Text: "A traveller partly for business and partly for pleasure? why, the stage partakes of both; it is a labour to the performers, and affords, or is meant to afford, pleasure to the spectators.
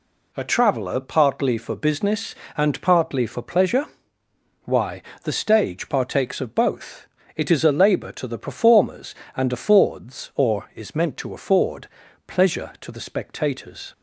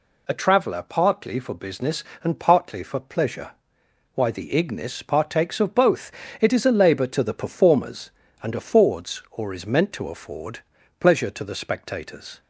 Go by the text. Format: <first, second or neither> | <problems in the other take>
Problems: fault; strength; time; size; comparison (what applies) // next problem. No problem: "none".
first | says "ignis" for "stage"; at 4.5 s